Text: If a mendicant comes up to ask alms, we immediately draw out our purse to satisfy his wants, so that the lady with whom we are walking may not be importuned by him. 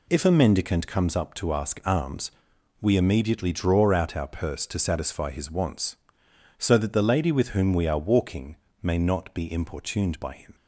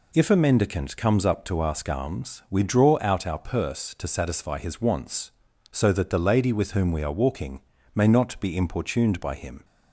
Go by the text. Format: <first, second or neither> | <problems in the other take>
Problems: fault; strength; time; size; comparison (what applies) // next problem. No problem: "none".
first | skips "immediately"; at 2.6 s // pauses between "walking" and "may"; slight; at 7.6 s; 0.34 s long; slight in the first